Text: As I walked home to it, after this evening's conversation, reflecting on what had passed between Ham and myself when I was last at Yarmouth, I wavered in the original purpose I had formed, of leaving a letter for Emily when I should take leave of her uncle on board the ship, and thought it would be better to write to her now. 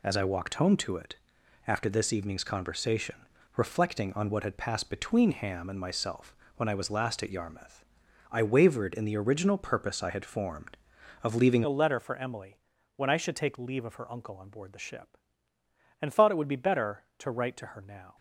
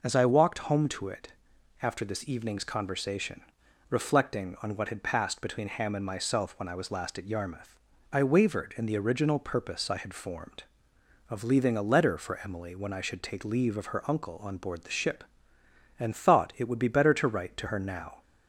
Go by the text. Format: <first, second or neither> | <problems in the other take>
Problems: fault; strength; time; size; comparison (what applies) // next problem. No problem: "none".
second | pauses between "myself" and "when"; slight; at 6.3 s; 0.22 s long // changes voice at "a"; from 11.6 s on; 6.5 s long // pauses between "Emily" and "when"; at 12.5 s; 0.40 s long